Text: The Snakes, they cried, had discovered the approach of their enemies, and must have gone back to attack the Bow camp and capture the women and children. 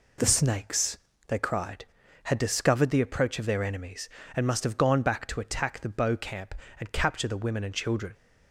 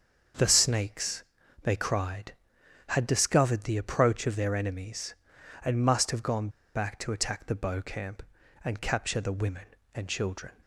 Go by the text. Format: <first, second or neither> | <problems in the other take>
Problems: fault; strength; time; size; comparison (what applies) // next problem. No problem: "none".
first | starts louder than the rest; until 1.7 s; 6.5 dB // pauses between "gone" and "back"; slight; at 6.4 s; 0.25 s long